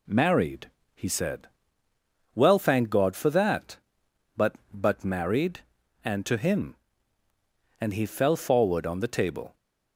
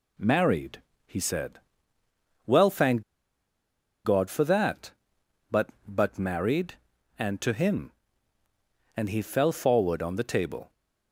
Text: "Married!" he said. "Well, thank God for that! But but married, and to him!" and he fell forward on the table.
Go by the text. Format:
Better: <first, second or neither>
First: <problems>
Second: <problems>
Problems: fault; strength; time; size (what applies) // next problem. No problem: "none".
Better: first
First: none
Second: pauses between "thank" and "God"; at 3.0 s; 1.0 s long